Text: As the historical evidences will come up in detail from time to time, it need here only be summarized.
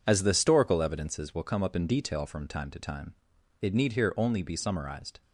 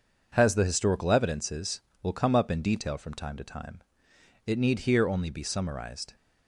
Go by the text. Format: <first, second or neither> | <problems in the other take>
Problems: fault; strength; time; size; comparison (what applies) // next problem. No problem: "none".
first | says "Has" for "As"; at 0.3 s